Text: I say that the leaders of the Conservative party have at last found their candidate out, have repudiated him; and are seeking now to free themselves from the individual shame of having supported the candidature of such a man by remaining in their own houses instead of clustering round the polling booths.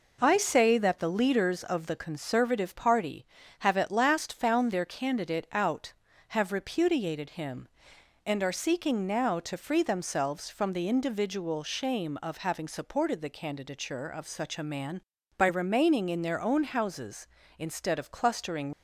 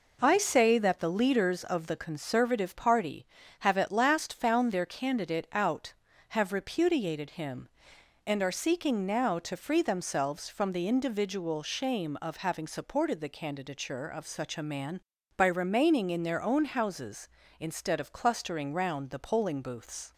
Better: second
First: stops before "round the polling booths"; at 18.7 s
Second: none

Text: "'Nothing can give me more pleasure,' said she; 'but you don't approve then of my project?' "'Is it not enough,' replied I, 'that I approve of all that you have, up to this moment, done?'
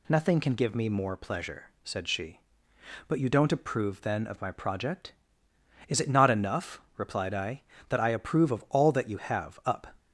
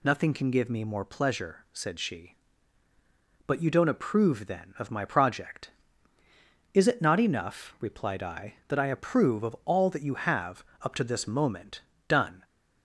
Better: second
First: stops before "to this moment done"; at 9.9 s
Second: none

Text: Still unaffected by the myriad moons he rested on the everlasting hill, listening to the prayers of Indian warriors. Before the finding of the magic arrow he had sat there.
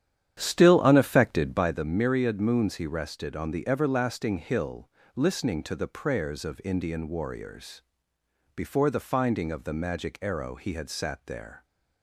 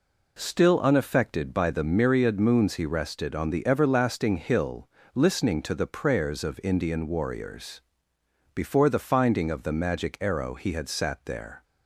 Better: second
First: starts louder than the rest; strong; until 1.8 s; 10 dB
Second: none

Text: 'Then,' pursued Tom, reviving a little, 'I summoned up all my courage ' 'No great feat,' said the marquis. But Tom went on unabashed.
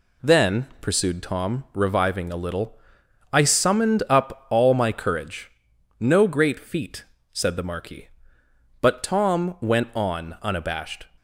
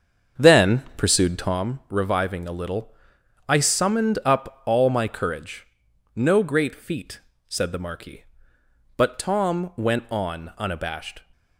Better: first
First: none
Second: starts louder than the rest; until 1.6 s; 7 dB

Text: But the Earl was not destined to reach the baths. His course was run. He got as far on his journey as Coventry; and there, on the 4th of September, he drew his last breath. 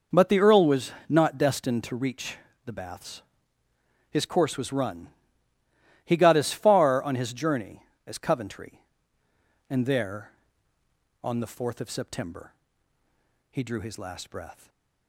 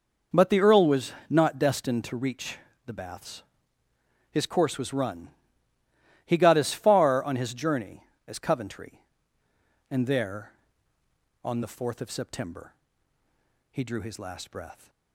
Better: neither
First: pauses between "was" and "not"; slight; at 0.9 s; 0.16 s long // pauses between "reach" and "the"; slight; at 2.3 s; 0.28 s long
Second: pauses between "was" and "not"; slight; at 1.1 s; 0.16 s long // pauses between "reach" and "the"; slight; at 2.5 s; 0.28 s long

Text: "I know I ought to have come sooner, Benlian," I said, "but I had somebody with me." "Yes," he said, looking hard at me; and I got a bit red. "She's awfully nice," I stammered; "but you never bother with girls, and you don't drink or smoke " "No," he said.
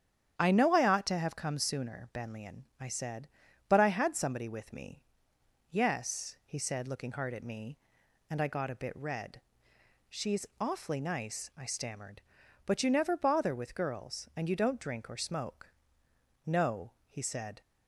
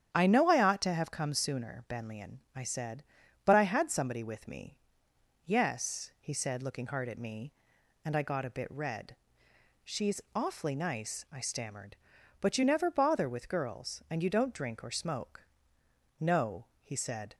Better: neither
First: starts louder than the rest; strong; until 1.3 s; 9 dB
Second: starts louder than the rest; strong; until 1.1 s; 9 dB

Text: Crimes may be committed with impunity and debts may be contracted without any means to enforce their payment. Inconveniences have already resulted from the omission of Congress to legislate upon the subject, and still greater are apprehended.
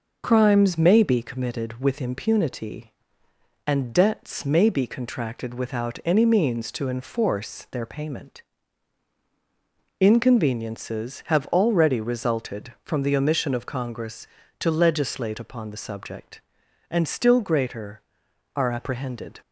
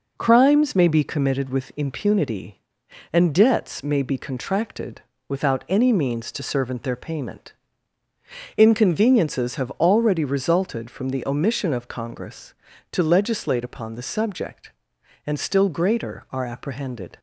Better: first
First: none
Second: pauses between "contracted" and "without"; slight; at 5.0 s; 0.26 s long // says "servant" for "enforce"; at 6.4 s

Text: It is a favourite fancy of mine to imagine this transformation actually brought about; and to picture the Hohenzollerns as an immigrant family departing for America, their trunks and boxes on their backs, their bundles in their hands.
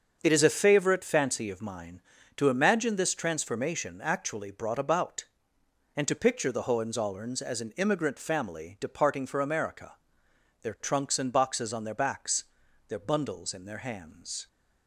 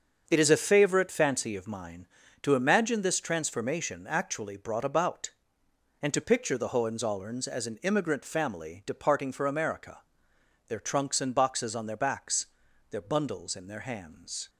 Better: neither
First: starts louder than the rest; until 1.2 s; 6.5 dB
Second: starts louder than the rest; until 1.2 s; 7 dB

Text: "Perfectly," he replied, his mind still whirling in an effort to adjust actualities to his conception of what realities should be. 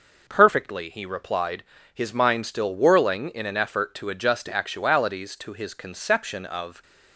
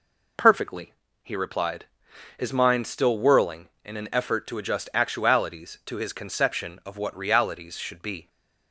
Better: second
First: stops before "what realities should be"; at 6.8 s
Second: none

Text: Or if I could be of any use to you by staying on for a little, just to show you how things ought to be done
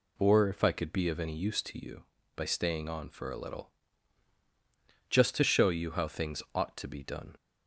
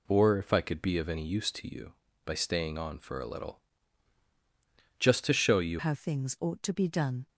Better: first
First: none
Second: changes voice at "how"; from 5.7 s on; 1.5 s long

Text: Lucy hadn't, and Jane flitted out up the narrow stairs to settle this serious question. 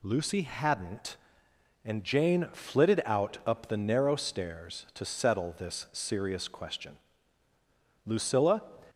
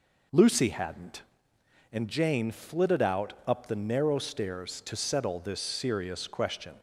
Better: second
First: goes on to say "Lucilla"; from 8.0 s on; 0.58 s long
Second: none

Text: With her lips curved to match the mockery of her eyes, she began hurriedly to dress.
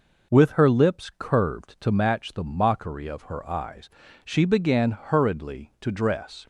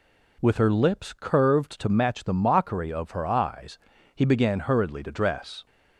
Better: first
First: none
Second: says "he" for "she"; at 4.1 s

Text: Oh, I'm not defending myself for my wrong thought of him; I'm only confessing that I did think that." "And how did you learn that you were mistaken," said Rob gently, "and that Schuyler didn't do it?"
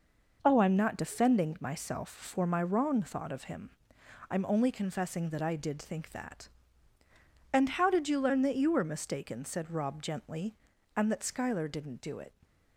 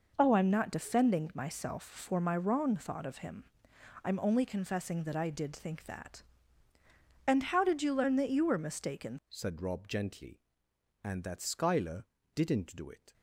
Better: first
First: none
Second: changes voice at "said"; from 9.2 s on; 3.9 s long // pauses between "Schuyler" and "didn't"; slight; at 12.0 s; 0.28 s long

